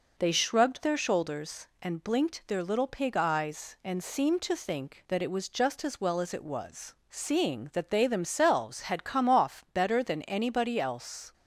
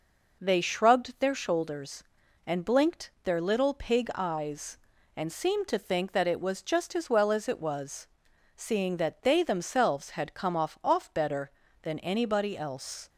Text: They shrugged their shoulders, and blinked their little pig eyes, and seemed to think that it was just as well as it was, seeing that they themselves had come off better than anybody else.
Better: first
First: none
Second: says "off" twice; at 10.8 s

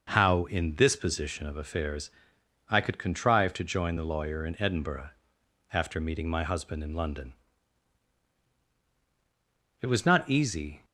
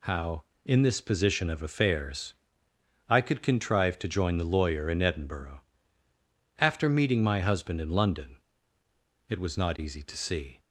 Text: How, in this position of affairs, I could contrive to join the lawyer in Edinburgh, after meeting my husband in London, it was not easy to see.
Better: second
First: stops before "to see"; at 10.8 s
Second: none

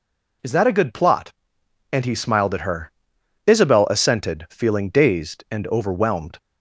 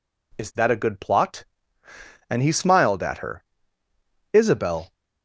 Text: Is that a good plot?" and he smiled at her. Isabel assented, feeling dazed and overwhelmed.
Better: first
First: none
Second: stops before "assented feeling dazed and overwhelmed"; at 4.9 s

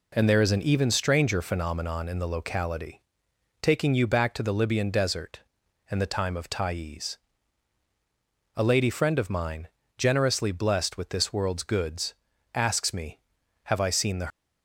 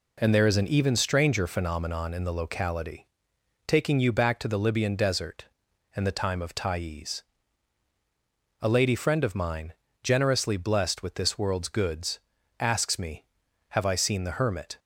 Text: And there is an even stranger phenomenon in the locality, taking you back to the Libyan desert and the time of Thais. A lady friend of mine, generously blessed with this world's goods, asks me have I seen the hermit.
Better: second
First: stops before "hermit"; at 14.2 s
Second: none

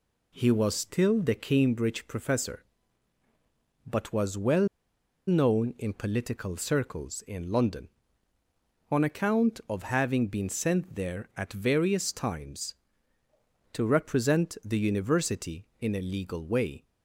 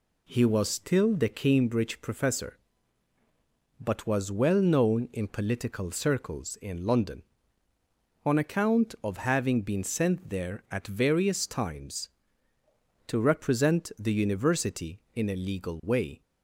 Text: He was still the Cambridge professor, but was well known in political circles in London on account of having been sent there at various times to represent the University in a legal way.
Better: second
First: pauses between "well" and "known"; noticeable; at 4.6 s; 0.60 s long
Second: none

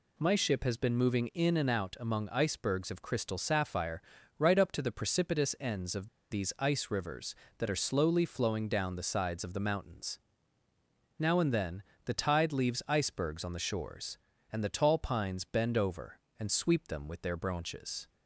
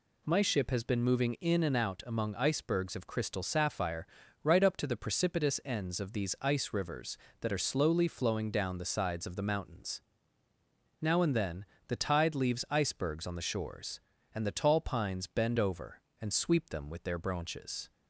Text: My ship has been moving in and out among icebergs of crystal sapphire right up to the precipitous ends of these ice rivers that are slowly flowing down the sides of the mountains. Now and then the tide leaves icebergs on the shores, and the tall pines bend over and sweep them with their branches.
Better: second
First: pauses between "sapphire" and "right"; at 4.0 s; 0.38 s long // pauses between "of" and "these"; slight; at 6.0 s; 0.24 s long // pauses between "then" and "the"; slight; at 11.8 s; 0.22 s long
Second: pauses between "sapphire" and "right"; at 4.0 s; 0.38 s long // pauses between "then" and "the"; slight; at 11.6 s; 0.22 s long

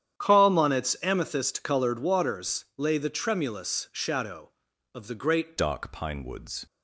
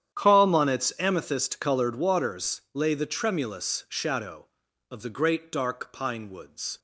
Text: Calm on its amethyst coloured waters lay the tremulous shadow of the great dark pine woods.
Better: second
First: starts louder than the rest; strong; until 1.2 s; 10 dB // changes voice at "dark"; from 5.5 s on; 1.1 s long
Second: starts louder than the rest; strong; until 1.2 s; 10 dB

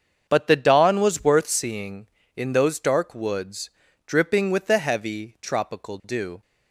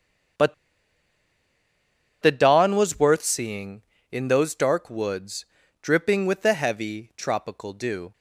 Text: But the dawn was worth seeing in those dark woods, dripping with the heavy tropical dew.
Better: first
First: starts louder than the rest; strong; until 1.3 s; 7 dB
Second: starts louder than the rest; strong; until 3.0 s; 7 dB // pauses between "But" and "the"; strong; at 0.5 s; 1.6 s long

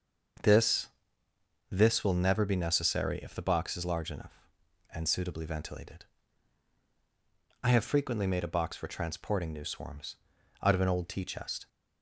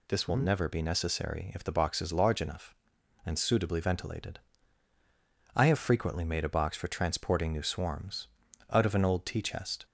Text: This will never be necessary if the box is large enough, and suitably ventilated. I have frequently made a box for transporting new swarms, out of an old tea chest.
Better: second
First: starts louder than the rest; noticeable; until 2.2 s; 6 dB // says "This" twice; at 1.6 s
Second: none

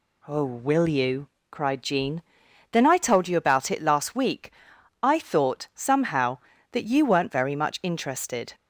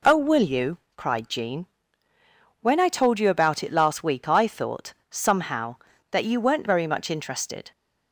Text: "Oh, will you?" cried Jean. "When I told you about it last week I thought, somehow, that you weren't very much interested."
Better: second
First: says "Then" for "When"; at 2.7 s // pauses between "week" and "I"; noticeable; at 4.5 s; 0.50 s long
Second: none

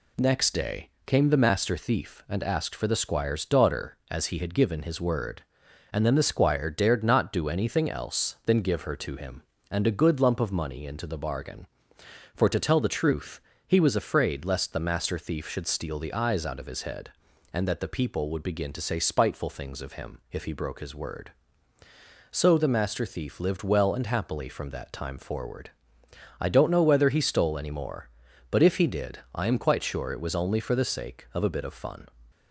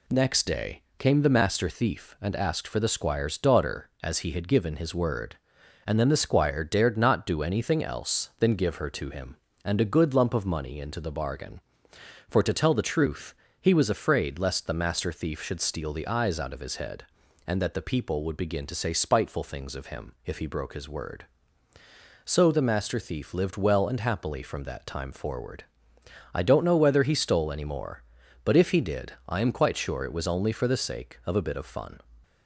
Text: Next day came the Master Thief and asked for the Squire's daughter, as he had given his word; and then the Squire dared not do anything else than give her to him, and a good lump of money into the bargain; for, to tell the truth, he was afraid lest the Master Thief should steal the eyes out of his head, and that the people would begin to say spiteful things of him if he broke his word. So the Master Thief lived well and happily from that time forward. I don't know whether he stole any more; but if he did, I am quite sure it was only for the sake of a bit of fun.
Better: neither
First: pauses between "day" and "came"; slight; at 0.9 s; 0.16 s long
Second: pauses between "day" and "came"; slight; at 0.8 s; 0.16 s long

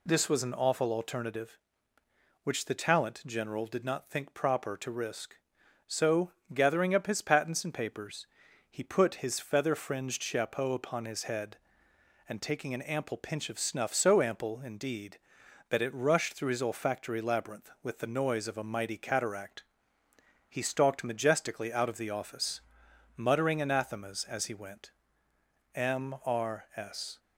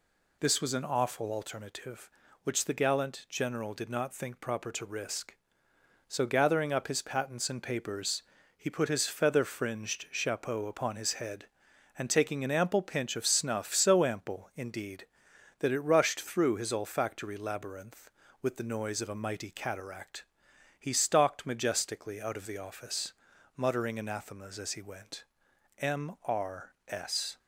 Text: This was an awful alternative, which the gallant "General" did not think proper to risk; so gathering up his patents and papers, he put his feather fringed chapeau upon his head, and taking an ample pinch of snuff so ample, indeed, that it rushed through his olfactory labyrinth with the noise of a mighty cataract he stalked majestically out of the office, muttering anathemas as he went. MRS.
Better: second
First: says "talent" for "gallant"; at 2.7 s // pauses between "so" and "gathering"; slight; at 6.3 s; 0.24 s long // pauses between "cataract" and "he"; noticeable; at 19.6 s; 0.84 s long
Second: pauses between "cataract" and "he"; noticeable; at 20.2 s; 0.54 s long

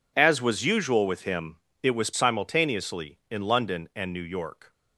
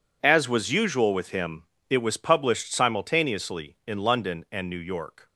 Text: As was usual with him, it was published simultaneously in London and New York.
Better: second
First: skips "published"; at 2.1 s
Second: none

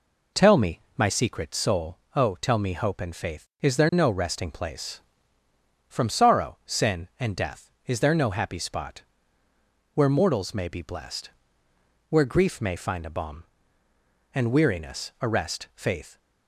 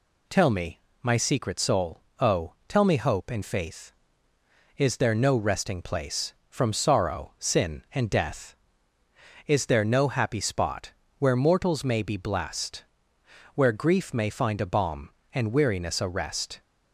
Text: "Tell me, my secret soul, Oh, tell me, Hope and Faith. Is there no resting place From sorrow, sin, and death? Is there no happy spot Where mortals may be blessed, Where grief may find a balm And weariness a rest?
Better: second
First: pauses between "spot" and "Where"; noticeable; at 9.0 s; 0.92 s long // goes on to say "Faith"; slight; from 15.7 s on; 0.44 s long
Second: pauses between "spot" and "Where"; slight; at 10.9 s; 0.26 s long

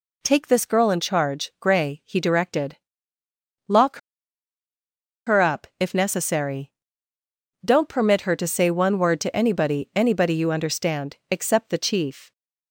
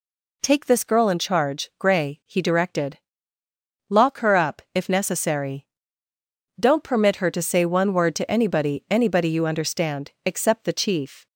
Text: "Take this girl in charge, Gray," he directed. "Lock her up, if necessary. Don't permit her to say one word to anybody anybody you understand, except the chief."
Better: second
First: pauses between "Lock" and "her"; strong; at 3.9 s; 1.2 s long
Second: none

